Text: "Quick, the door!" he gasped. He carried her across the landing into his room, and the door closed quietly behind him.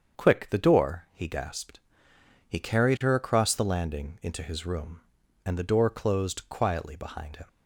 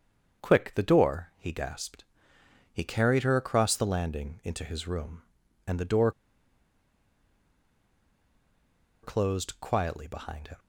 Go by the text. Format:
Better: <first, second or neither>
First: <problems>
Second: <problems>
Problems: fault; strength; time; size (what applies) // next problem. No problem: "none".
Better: first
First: starts louder than the rest; strong; until 1.2 s; 7 dB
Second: starts louder than the rest; strong; until 1.4 s; 7 dB // pauses between "door" and "closed"; strong; at 6.1 s; 2.9 s long